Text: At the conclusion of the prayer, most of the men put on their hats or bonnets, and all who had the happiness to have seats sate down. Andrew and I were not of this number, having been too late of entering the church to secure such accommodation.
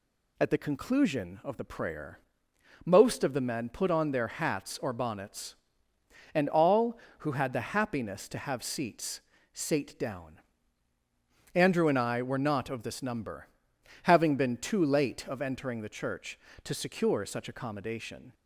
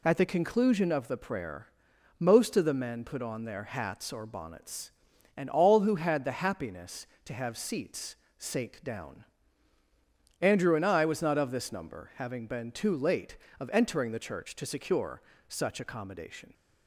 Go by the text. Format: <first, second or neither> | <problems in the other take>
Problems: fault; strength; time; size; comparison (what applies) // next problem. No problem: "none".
first | pauses between "seats" and "sate"; slight; at 8.1 s; 0.22 s long; slight in the first // says "was" for "were"; at 11.0 s // pauses between "secure" and "such"; slight; at 15.2 s; 0.28 s long